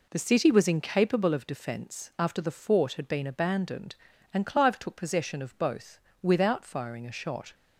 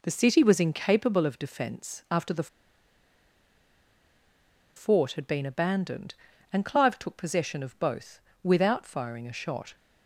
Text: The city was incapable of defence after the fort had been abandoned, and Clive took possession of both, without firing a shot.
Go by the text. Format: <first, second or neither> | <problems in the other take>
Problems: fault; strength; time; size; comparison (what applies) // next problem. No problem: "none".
first | pauses between "the" and "fort"; strong; at 2.4 s; 2.2 s long